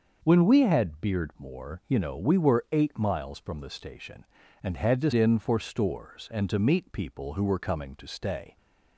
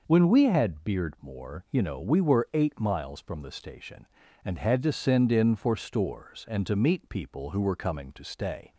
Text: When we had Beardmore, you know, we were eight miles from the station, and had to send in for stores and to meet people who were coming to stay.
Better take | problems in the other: second | starts louder than the rest; until 1.2 s; 6 dB // skips "send"; at 5.1 s

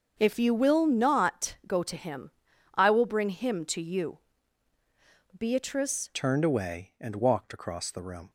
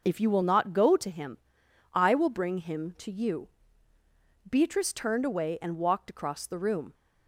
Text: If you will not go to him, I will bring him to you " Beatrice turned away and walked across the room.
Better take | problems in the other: second | starts louder than the rest; until 1.1 s; 7 dB; noticeable in the second // changes voice at "turned"; from 6.1 s on; 2.1 s long

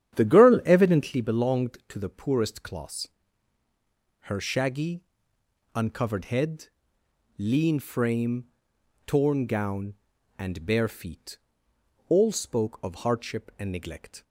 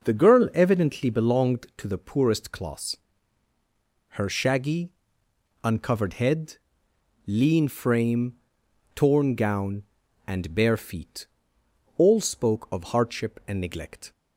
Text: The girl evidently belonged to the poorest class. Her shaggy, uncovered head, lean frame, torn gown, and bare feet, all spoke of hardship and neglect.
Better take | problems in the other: second | starts louder than the rest; strong; until 1.2 s; 10 dB

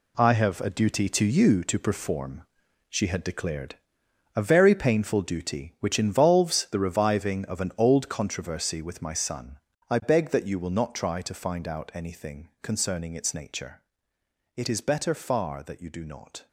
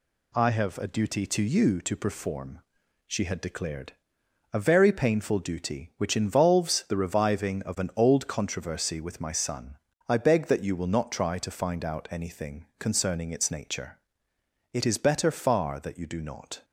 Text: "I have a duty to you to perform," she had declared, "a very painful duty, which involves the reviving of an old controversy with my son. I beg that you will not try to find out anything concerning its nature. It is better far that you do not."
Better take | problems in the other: second | gets quieter; strong; throughout; 10 dB

